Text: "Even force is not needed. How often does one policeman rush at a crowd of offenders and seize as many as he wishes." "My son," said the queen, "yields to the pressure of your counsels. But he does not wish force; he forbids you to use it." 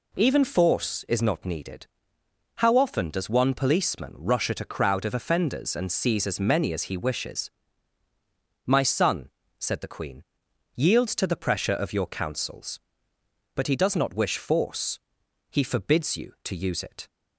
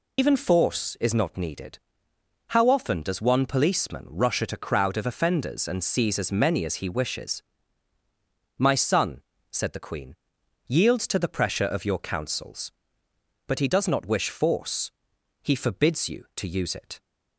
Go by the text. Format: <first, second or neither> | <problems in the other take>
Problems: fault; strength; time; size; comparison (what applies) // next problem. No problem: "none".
first | loses the start of "Even"; at 0.1 s; 125 ms